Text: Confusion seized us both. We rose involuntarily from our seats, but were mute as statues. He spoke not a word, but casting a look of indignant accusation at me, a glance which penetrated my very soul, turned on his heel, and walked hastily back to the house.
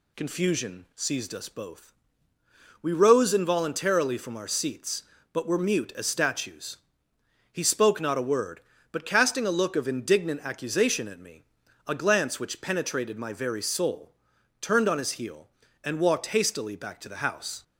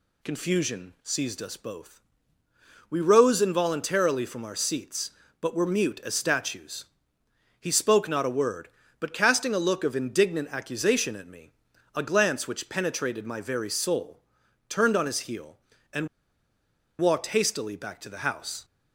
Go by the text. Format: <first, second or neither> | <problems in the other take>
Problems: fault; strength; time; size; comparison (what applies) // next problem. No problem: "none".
first | pauses between "and" and "walked"; noticeable; at 16.0 s; 0.91 s long